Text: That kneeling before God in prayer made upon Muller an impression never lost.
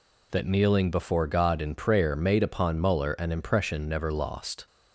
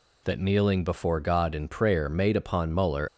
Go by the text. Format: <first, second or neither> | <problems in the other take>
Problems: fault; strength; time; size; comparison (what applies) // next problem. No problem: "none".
first | stops before "an impression never lost"; at 3.0 s